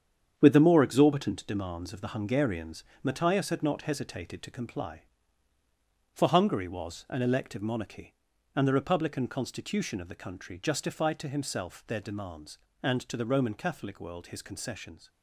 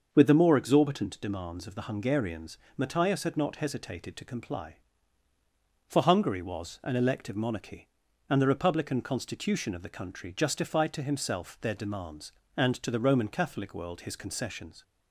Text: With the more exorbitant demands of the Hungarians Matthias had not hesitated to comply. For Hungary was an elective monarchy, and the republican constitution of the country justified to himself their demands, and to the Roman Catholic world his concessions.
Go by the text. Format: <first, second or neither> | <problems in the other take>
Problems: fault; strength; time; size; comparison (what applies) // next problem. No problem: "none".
second | gets quieter; strong; throughout; 7.5 dB // starts louder than the rest; strong; until 1.3 s; 8 dB; also in the second // pauses between "Hungarians" and "Matthias"; slight; at 2.8 s; 0.20 s long; slight in the second